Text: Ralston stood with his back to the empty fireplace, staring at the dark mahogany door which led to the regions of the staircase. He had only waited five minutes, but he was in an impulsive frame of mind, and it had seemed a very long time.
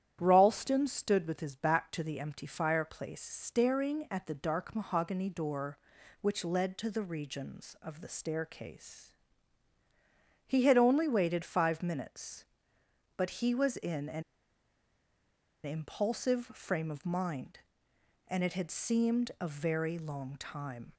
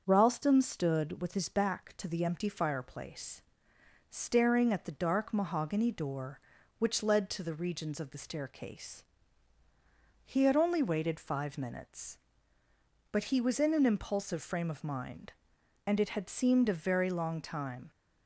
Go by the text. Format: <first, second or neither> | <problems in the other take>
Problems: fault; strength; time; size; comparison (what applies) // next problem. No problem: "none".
second | starts louder than the rest; strong; until 1.2 s; 10 dB; also in the second // pauses between "an" and "impulsive"; strong; at 14.2 s; 1.4 s long